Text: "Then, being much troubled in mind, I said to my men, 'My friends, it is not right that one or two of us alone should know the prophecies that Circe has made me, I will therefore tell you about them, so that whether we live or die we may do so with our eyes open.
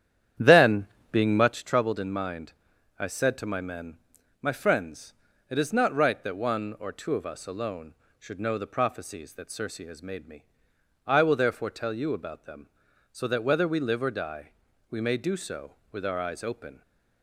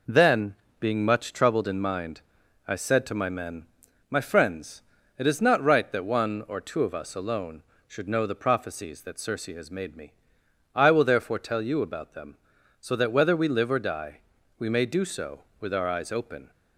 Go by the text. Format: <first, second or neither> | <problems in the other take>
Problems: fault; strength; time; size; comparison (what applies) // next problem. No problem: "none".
second | starts louder than the rest; strong; until 1.6 s; 10 dB // pauses between "die" and "we"; at 14.5 s; 0.40 s long; also in the second